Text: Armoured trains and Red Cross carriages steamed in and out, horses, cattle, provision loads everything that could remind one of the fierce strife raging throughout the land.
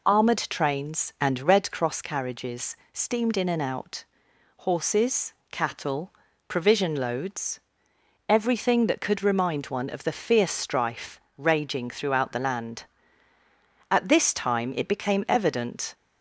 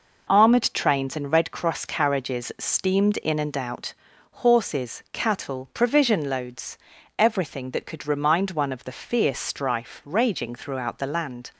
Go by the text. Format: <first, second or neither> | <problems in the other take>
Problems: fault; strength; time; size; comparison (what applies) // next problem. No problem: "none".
second | pauses between "carriages" and "steamed"; slight; at 2.7 s; 0.16 s long // pauses between "loads" and "everything"; noticeable; at 7.5 s; 0.70 s long; also in the second // pauses between "strife" and "raging"; slight; at 11.1 s; 0.18 s long // goes on to say "At this time it became evident"; strong; from 13.9 s on; 2.0 s long